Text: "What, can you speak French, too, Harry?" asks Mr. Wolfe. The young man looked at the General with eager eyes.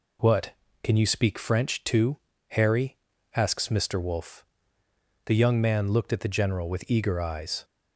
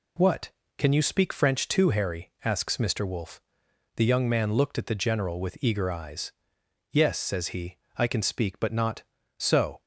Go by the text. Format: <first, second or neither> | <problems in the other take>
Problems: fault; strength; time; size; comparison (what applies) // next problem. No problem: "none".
first | goes on to say "Yes says he I can speak but not so"; strong; from 6.8 s on; 2.9 s long